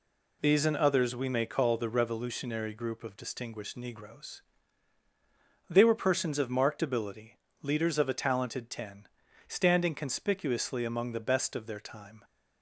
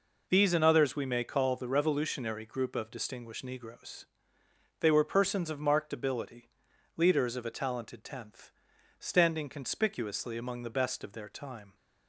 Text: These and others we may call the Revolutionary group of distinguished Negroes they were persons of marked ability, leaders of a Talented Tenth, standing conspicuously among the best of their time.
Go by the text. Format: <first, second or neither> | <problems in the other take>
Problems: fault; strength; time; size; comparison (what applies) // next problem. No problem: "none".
second | pauses between "Negroes" and "they"; strong; at 4.4 s; 1.2 s long; noticeable in the second // says "Ten" for "Tenth"; at 8.7 s